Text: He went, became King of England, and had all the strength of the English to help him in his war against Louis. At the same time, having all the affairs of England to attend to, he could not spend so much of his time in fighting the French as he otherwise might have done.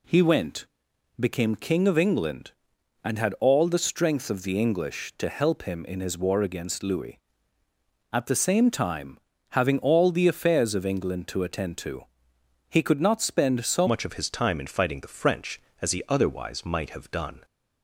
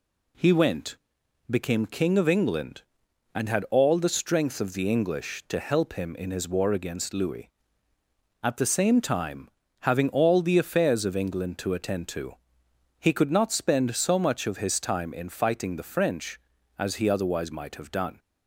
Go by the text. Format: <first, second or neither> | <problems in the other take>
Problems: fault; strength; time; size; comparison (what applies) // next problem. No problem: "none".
second | changes voice at "much"; from 13.8 s on; 3.6 s long